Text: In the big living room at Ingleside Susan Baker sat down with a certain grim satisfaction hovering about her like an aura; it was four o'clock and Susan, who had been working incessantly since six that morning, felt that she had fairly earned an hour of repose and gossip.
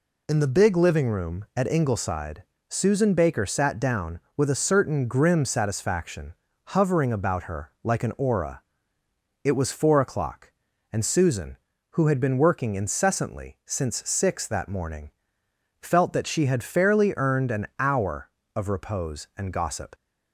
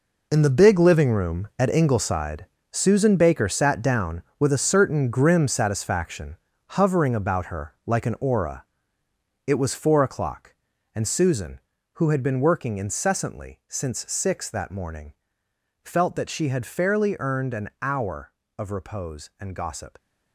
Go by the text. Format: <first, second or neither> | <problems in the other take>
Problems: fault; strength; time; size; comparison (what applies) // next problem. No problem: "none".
first | gets quieter; strong; throughout; 11 dB // pauses between "Ingleside" and "Susan"; slight; at 2.4 s; 0.26 s long; slight in the first // pauses between "satisfaction" and "hovering"; slight; at 6.3 s; 0.34 s long; slight in the first